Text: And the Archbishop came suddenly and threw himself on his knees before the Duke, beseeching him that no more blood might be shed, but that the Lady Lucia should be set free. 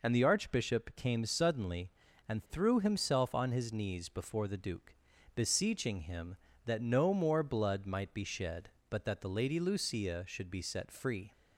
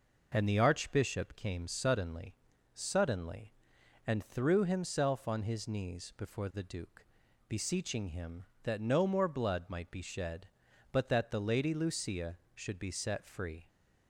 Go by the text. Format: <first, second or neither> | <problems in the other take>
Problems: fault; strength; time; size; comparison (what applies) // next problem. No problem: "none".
first | says "suddenly" twice; at 2.7 s